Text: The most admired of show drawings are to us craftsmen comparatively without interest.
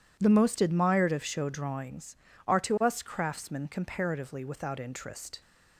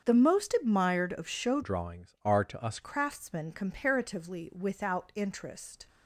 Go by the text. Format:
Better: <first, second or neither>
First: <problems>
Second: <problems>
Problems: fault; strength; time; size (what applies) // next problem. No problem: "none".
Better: first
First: none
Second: starts louder than the rest; strong; until 1.1 s; 7 dB // changes voice from "drawings" to "us"; from 1.6 to 2.7 s; 1.1 s long